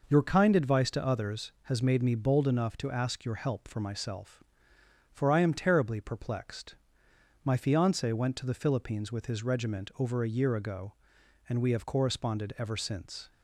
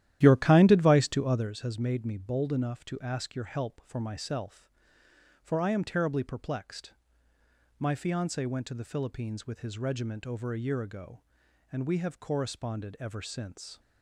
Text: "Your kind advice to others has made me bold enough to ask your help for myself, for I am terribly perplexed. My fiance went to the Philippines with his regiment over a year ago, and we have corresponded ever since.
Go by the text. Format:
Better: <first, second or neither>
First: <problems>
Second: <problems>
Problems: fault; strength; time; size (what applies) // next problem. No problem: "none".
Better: first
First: none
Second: starts louder than the rest; strong; until 1.5 s; 12.5 dB